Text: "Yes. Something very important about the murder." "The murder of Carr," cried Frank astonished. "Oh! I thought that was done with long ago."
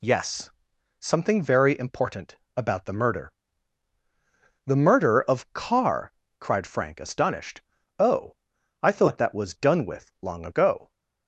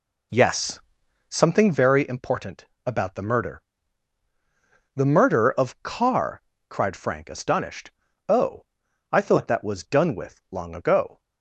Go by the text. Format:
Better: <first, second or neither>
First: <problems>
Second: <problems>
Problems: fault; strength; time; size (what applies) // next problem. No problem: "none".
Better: first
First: pauses between "important" and "about"; slight; at 2.3 s; 0.20 s long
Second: starts louder than the rest; slight; until 1.9 s; 2.5 dB // pauses between "important" and "about"; slight; at 2.6 s; 0.20 s long